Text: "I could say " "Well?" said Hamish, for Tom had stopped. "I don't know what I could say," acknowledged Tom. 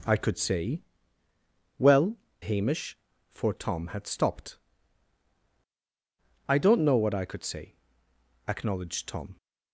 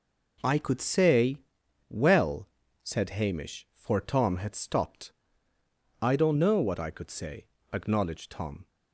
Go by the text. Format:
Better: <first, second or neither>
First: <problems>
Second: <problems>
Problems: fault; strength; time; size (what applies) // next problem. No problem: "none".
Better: second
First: skips "said"; at 2.2 s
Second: none